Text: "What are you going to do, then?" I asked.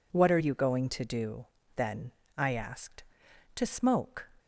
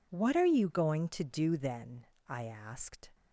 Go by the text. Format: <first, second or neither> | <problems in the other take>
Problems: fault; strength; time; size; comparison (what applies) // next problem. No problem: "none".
second | goes on to say "To smoke"; noticeable; from 3.5 s on; 0.74 s long